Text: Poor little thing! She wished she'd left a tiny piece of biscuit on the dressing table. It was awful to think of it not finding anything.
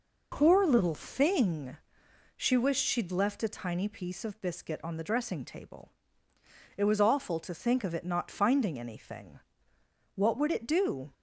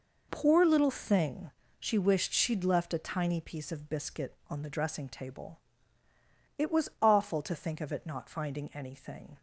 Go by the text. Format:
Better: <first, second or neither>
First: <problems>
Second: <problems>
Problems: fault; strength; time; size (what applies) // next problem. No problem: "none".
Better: second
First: goes on to say "What would it do"; noticeable; from 10.1 s on; 0.96 s long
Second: none